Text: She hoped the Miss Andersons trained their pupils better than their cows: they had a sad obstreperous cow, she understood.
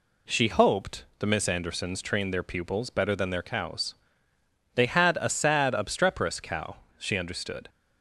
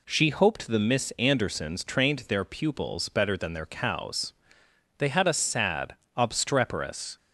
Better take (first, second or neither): first